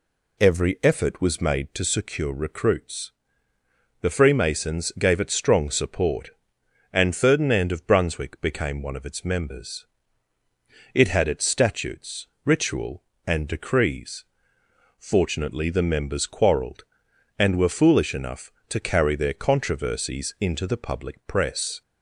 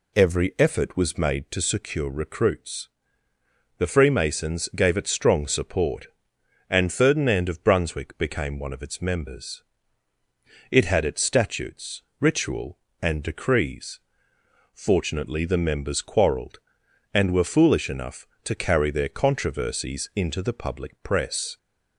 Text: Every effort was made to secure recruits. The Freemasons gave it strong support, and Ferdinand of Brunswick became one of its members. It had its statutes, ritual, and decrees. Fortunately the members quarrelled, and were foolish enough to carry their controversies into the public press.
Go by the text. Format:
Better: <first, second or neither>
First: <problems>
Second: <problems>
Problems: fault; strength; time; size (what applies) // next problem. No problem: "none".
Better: neither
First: none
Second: none